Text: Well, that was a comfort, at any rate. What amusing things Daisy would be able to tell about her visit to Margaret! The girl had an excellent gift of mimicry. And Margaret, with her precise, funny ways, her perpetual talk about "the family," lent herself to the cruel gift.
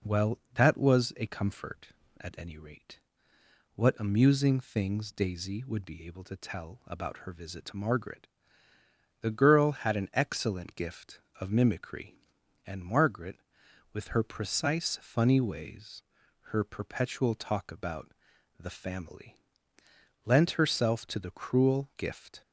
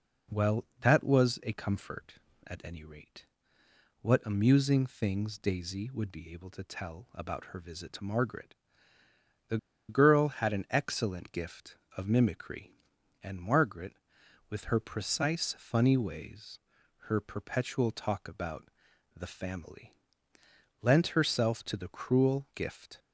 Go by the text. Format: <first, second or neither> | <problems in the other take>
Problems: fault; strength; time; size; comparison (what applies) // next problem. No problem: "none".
first | pauses between "The" and "girl"; slight; at 9.5 s; 0.31 s long // pauses between "about" and "the"; noticeable; at 18.6 s; 0.46 s long; noticeable in the first